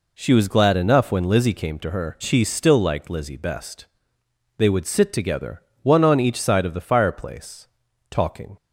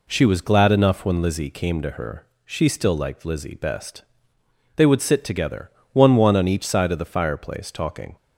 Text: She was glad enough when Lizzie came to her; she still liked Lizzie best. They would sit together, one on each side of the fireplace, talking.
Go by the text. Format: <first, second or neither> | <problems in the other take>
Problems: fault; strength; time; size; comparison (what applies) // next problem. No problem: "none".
first | says "one" twice; at 6.1 s